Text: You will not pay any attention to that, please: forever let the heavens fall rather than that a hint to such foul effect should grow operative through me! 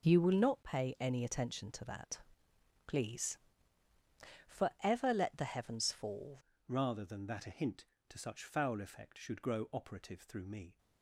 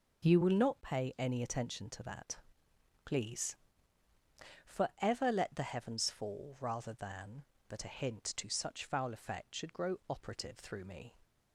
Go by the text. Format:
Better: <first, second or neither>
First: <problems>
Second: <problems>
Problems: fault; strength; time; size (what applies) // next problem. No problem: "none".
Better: second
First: changes voice at "rather"; from 6.6 s on; 4.1 s long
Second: none